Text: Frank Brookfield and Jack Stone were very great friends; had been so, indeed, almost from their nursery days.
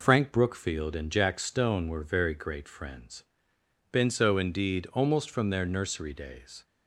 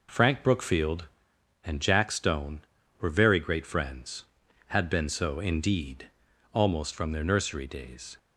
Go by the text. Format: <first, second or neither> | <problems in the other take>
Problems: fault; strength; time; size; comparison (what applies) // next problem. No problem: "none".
second | skips "had"; at 3.5 s